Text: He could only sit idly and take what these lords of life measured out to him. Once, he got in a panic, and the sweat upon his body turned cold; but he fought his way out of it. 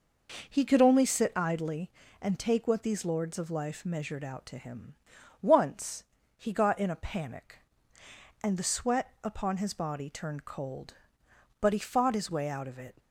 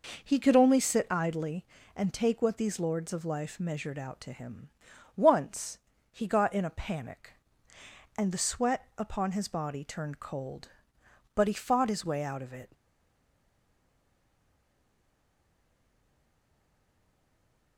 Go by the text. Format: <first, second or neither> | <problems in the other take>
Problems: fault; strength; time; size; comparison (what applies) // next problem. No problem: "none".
first | stays silent after the last word; strong; from 12.7 s on; 5.0 s long